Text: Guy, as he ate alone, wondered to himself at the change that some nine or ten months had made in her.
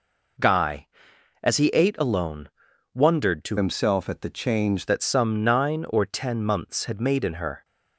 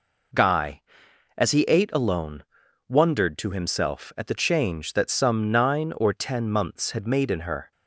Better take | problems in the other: second | changes voice from "himself" to "change"; from 3.5 to 4.8 s; 1.3 s long

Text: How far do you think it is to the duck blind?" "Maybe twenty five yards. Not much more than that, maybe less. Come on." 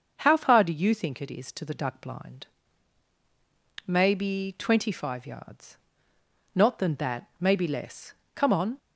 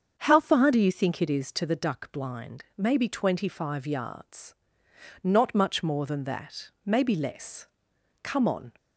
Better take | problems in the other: second | starts louder than the rest; until 1.1 s; 6.5 dB; strong in the second // skips "much more"; at 6.7 s

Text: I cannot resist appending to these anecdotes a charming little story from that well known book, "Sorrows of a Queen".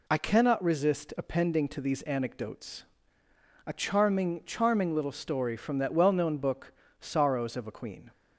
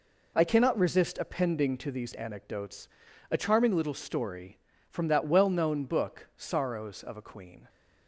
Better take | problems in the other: second | pauses between "anecdotes" and "a"; noticeable; at 2.8 s; 0.84 s long; also in the second // says "charming" twice; at 4.4 s

